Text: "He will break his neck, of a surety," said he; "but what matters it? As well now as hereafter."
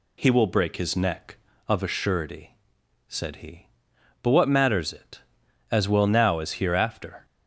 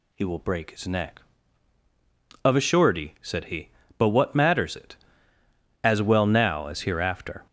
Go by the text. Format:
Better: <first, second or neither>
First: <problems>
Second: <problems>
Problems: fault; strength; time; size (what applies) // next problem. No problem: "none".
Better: neither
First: none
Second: none